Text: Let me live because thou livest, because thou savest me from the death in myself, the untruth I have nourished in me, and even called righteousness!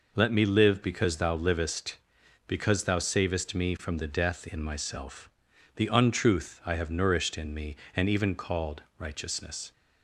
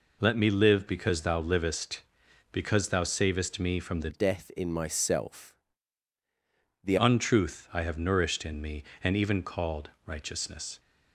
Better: first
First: pauses between "called" and "righteousness"; slight; at 8.8 s; 0.16 s long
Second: changes voice from "death" to "the"; from 4.1 to 6.9 s; 2.8 s long // pauses between "called" and "righteousness"; slight; at 9.8 s; 0.16 s long

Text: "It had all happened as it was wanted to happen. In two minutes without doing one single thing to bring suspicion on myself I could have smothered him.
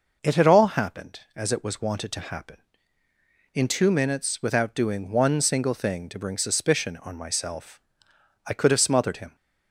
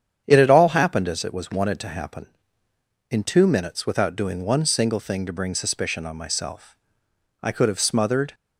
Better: first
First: pauses between "myself" and "I"; noticeable; at 7.7 s; 0.66 s long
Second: starts louder than the rest; strong; until 1.2 s; 9 dB // pauses between "myself" and "I"; noticeable; at 6.7 s; 0.66 s long // stops before "him"; at 8.3 s

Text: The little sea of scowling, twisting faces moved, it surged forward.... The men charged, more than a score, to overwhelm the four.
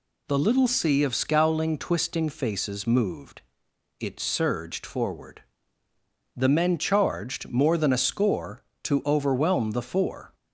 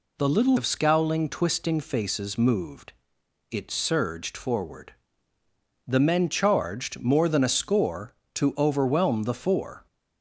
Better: first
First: none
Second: skips "sea"; at 0.5 s

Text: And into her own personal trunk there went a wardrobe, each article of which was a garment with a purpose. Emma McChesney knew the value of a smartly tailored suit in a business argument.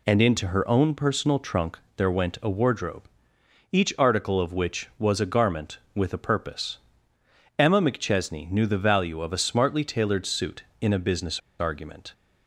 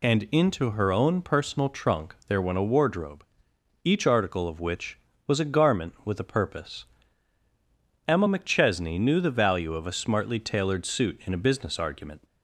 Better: second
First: pauses between "trunk" and "there"; slight; at 1.7 s; 0.16 s long // pauses between "business" and "argument"; slight; at 11.3 s; 0.19 s long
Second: none

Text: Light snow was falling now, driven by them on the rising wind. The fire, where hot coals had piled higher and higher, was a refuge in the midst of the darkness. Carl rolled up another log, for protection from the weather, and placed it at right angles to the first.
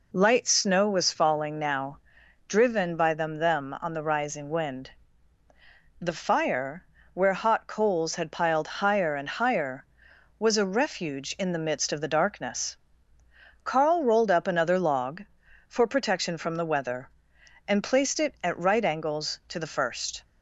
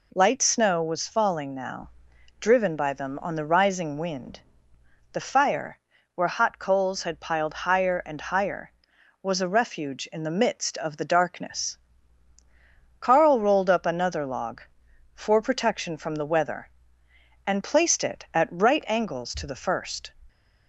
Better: second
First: says "them" twice; at 3.3 s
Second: none

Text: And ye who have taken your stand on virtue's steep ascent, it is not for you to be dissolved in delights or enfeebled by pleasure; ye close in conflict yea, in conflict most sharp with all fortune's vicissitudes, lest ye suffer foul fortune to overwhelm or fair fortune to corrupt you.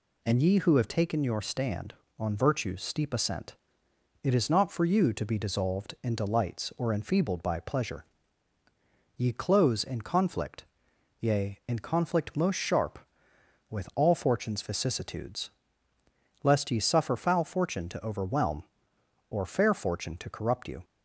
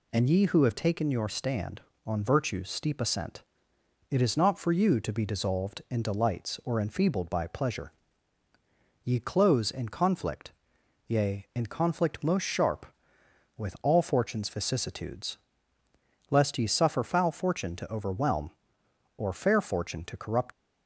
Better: first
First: pauses between "conflict" and "yea"; noticeable; at 10.6 s; 0.54 s long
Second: pauses between "conflict" and "yea"; noticeable; at 10.5 s; 0.54 s long // stops before "you"; at 20.5 s

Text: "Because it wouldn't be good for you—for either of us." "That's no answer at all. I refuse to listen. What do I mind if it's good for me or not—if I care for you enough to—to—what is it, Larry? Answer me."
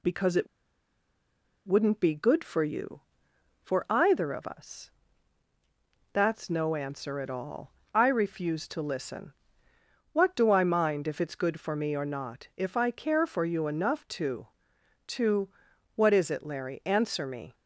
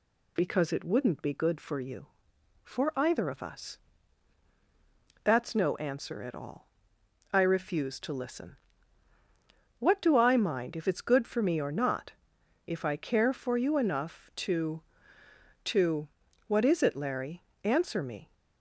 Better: second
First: pauses between "it" and "wouldn't"; at 0.4 s; 1.2 s long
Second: none

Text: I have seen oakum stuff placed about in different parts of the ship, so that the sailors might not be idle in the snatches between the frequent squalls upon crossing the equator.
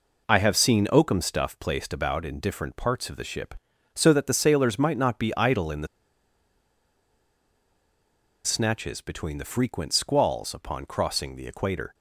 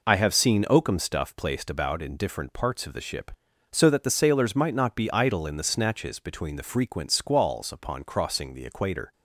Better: second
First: pauses between "the" and "snatches"; strong; at 5.8 s; 2.5 s long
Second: none

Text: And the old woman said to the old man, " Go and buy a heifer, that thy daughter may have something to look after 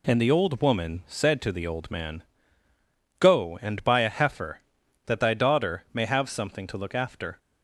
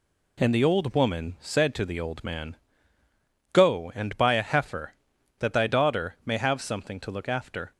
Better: neither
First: none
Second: none

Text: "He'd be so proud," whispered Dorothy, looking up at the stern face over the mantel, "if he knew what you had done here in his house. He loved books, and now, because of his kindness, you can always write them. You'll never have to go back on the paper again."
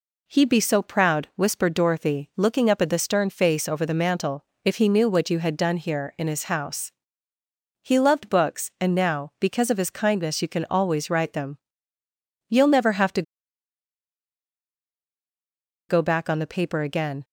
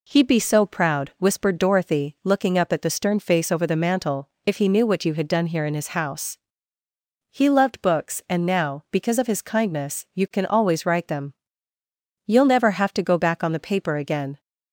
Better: second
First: pauses between "to" and "go"; strong; at 13.2 s; 2.6 s long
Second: none

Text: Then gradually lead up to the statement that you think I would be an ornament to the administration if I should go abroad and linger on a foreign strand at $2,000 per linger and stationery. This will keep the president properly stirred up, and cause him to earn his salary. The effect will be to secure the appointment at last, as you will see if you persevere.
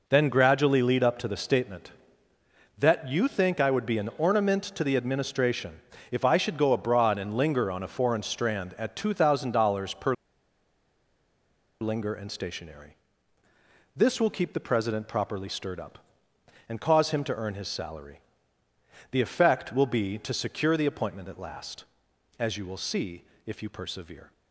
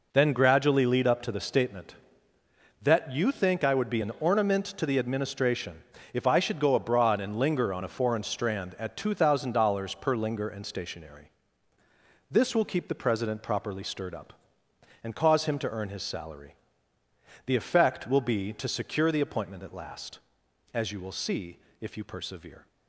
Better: second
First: pauses between "administration" and "if"; slight; at 5.8 s; 0.30 s long // pauses between "per" and "linger"; strong; at 10.1 s; 1.6 s long // pauses between "see" and "if"; slight; at 23.2 s; 0.22 s long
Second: pauses between "administration" and "if"; slight; at 5.8 s; 0.30 s long // pauses between "see" and "if"; slight; at 21.5 s; 0.22 s long

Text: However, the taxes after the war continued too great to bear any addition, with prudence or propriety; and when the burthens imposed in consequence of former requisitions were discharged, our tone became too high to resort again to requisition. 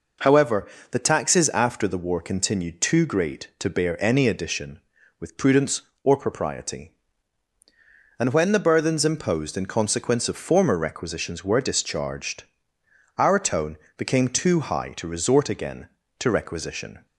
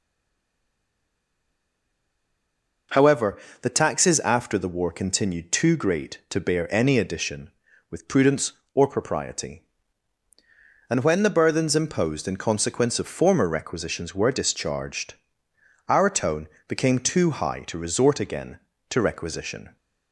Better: first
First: pauses between "tone" and "became"; slight; at 13.7 s; 0.18 s long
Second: stays silent before the first word; strong; until 2.8 s; 2.8 s long // pauses between "tone" and "became"; slight; at 16.4 s; 0.18 s long

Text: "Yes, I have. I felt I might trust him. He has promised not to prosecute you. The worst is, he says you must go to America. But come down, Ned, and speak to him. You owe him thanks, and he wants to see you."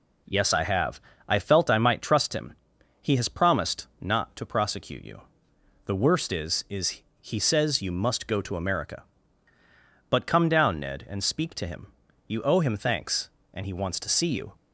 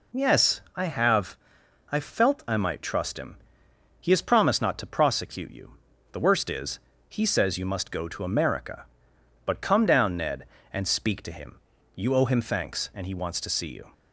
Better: second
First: says "is" twice; at 6.6 s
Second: none

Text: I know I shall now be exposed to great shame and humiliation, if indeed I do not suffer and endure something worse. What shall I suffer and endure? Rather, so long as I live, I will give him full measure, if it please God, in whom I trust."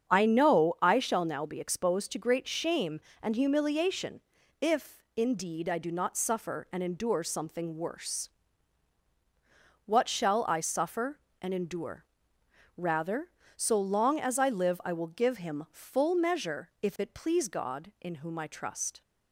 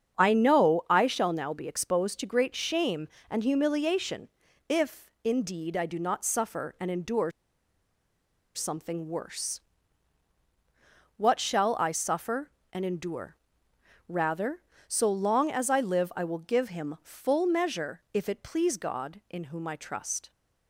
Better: first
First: starts louder than the rest; strong; until 1.1 s; 7.5 dB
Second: starts louder than the rest; strong; until 1.2 s; 7.5 dB // pauses between "endure" and "something"; at 7.3 s; 1.2 s long

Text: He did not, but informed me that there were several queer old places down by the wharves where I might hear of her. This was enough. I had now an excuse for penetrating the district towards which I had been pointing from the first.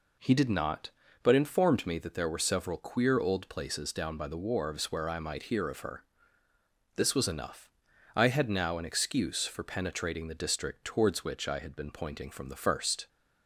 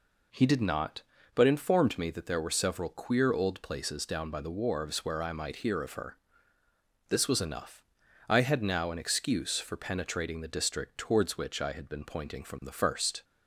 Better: neither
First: none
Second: none

